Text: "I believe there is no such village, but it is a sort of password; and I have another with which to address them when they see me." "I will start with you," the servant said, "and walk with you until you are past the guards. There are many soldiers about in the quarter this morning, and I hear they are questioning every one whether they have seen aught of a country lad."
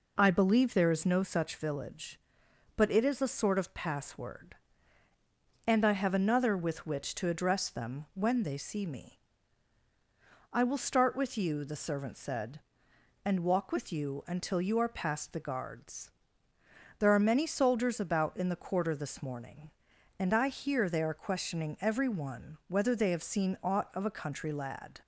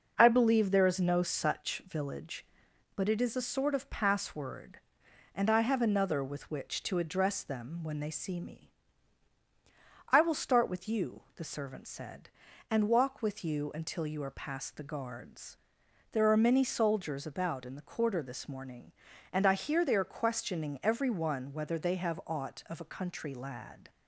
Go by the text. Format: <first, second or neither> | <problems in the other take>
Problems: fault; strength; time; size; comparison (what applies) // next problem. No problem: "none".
first | skips "seen"; at 22.2 s